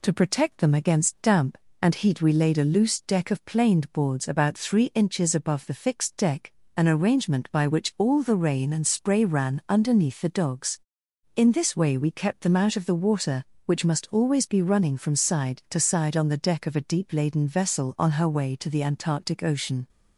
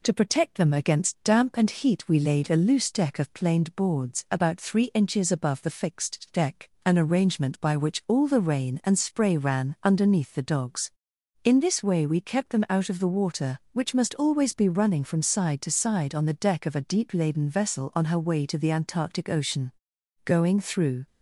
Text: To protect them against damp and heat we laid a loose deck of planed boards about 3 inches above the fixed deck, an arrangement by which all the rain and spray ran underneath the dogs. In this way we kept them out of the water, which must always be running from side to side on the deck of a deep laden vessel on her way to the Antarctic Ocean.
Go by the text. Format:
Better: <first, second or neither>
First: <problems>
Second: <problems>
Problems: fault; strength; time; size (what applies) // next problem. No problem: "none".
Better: first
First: none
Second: goes on to say "Going through"; noticeable; from 20.2 s on; 0.82 s long